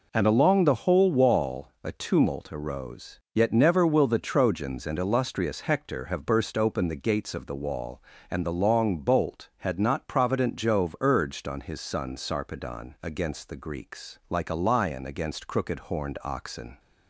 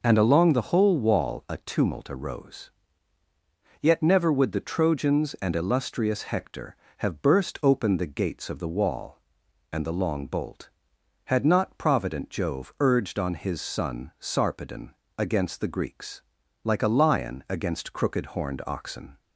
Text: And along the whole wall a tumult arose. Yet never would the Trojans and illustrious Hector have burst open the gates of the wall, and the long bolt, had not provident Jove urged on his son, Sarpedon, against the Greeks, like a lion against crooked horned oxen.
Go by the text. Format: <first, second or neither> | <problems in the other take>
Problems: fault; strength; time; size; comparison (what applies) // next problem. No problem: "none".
second | says "will" for "would"; at 3.8 s